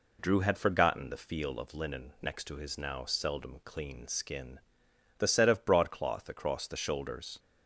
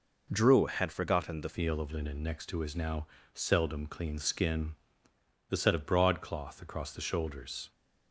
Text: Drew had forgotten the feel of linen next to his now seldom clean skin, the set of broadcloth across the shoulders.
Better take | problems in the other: first | changes voice at "feel"; from 1.5 s on; 6.2 s long // pauses between "now" and "seldom"; slight; at 3.0 s; 0.26 s long

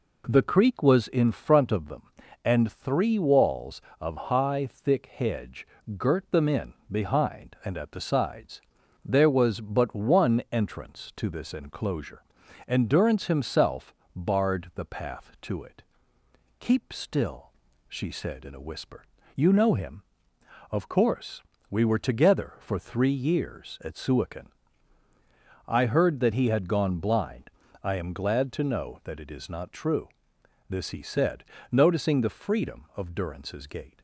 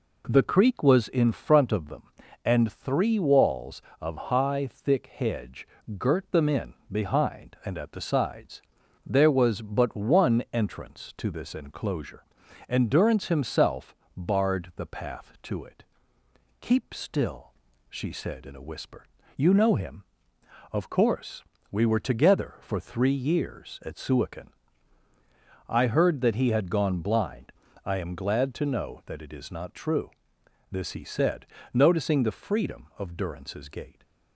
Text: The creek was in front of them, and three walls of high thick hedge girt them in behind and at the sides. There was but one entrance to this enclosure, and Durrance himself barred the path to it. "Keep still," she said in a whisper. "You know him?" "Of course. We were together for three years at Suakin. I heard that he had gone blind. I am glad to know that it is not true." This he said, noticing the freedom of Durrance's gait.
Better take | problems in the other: neither | pauses between "hedge" and "girt"; slight; the same in both // pauses between "in" and "behind"; slight; the same in both // pauses between "himself" and "barred"; slight; the same in both

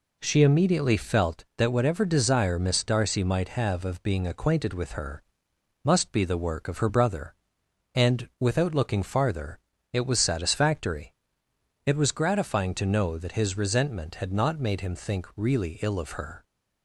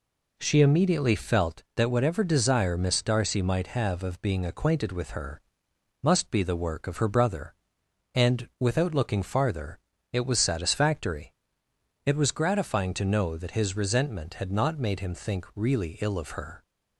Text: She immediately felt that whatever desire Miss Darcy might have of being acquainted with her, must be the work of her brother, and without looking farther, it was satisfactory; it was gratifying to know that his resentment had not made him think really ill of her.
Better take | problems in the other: neither | none

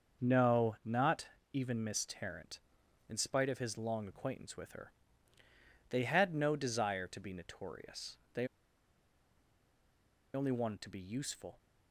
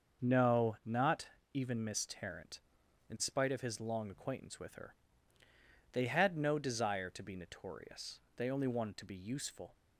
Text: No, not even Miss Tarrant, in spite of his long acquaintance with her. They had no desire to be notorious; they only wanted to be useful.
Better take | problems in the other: second | starts louder than the rest; until 1.5 s; 6.5 dB; also in the second // pauses between "not" and "even"; slight; at 1.2 s; 0.26 s long; slight in the second // pauses between "they" and "only"; strong; at 8.4 s; 1.8 s long

